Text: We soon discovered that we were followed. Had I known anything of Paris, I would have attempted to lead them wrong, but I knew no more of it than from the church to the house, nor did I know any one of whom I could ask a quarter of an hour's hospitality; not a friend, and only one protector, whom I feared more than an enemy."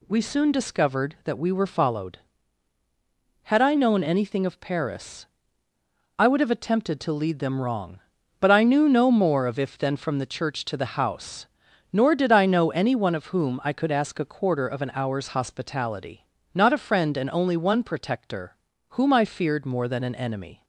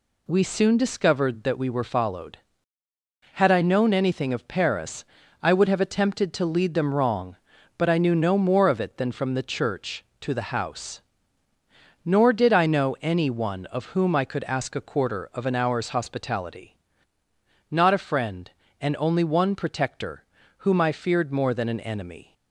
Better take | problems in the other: second | says "if" for "it"; at 9.5 s

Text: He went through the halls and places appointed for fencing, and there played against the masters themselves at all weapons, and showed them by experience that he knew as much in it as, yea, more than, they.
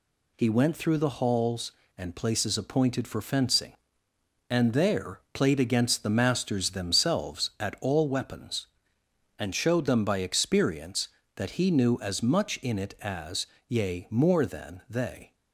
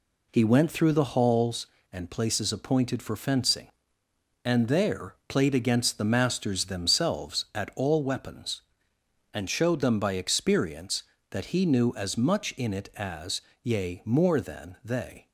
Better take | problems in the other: first | starts louder than the rest; slight; until 1.7 s; 2.5 dB

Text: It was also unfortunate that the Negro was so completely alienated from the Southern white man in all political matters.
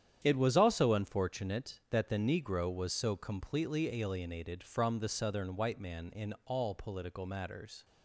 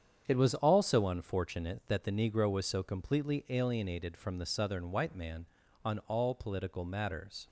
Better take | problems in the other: first | starts louder than the rest; strong; until 1.2 s; 8 dB; strong in the first // says "on" for "in"; at 5.8 s

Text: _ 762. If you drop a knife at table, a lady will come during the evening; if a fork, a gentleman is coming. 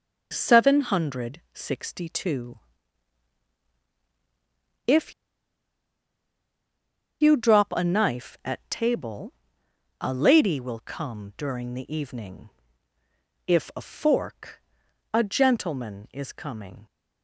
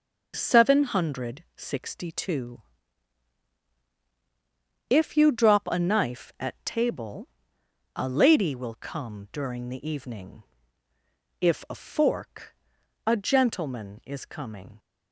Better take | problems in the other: second | pauses between "If" and "you"; strong; at 5.1 s; 2.0 s long

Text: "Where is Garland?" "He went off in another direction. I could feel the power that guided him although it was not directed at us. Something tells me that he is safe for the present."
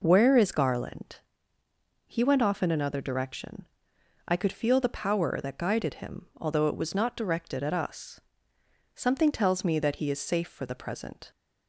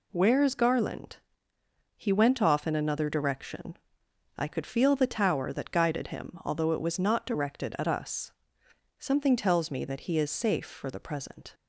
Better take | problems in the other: first | says "tower" for "power"; at 5.0 s

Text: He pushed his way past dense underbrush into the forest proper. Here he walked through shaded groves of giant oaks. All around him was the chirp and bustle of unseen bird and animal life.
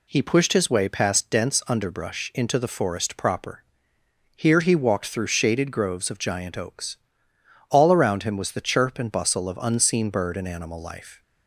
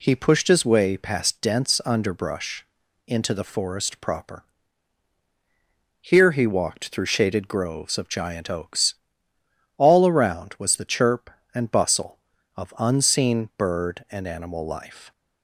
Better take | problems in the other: first | pauses between "underbrush" and "into"; at 2.6 s; 0.40 s long // skips "him"; at 10.5 s

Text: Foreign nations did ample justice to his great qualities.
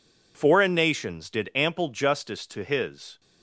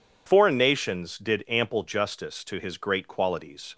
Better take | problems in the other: second | stops before "great qualities"; at 3.1 s

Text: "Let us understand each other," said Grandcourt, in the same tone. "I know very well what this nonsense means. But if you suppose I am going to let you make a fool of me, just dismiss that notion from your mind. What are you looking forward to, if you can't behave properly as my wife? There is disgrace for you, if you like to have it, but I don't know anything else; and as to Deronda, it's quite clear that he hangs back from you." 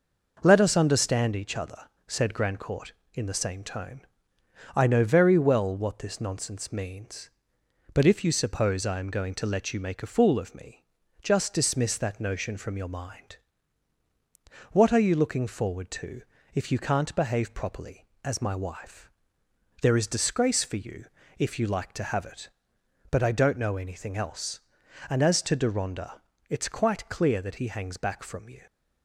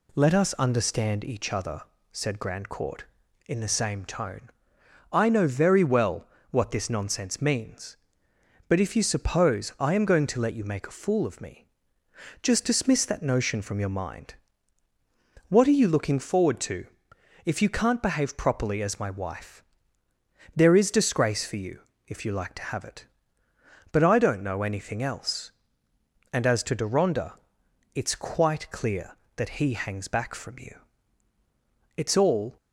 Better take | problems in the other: first | pauses between "well" and "what"; slight; at 6.2 s; 0.24 s long // goes on to say "It's all"; from 31.9 s on; 0.60 s long

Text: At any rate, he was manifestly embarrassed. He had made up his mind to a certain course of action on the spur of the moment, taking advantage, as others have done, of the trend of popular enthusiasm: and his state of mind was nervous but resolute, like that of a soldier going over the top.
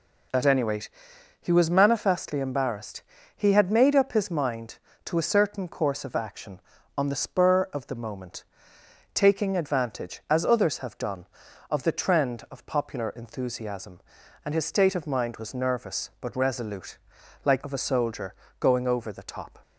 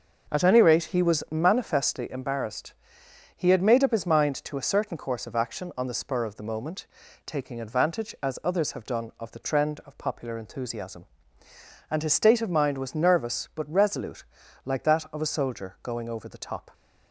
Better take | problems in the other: second | skips "that"; at 17.6 s // pauses between "soldier" and "going"; slight; at 18.3 s; 0.26 s long

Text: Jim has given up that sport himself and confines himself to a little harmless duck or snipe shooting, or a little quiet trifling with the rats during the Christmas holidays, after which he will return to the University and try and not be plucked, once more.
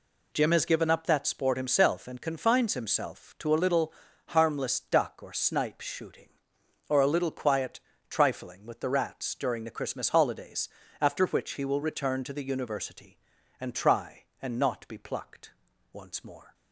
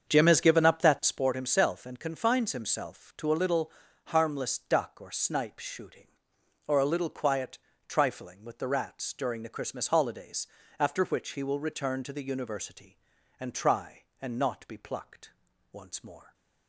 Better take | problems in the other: first | starts louder than the rest; strong; until 1.3 s; 7 dB // pauses between "little" and "harmless"; slight; at 3.7 s; 0.34 s long; slight in the first // pauses between "quiet" and "trifling"; slight; at 7.5 s; 0.30 s long; slight in the first

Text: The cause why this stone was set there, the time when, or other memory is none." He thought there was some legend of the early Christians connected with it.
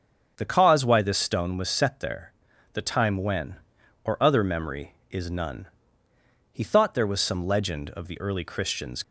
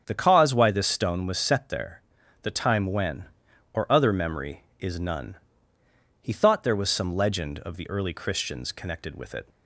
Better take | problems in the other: second | starts louder than the rest; strong; until 1.3 s; 7.5 dB; strong in the second // stops before "connected with it"; at 9.0 s

